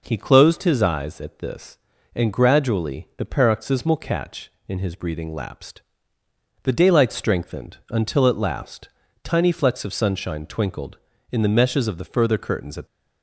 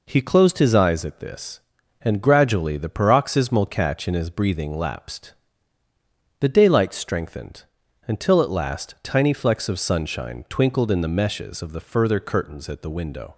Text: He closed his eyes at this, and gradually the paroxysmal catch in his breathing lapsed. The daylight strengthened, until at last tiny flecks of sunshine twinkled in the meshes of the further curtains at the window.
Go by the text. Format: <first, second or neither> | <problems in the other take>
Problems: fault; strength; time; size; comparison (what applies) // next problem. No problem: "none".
second | pauses between "last" and "tiny"; slight; at 8.8 s; 0.34 s long // stops before "the window"; at 12.8 s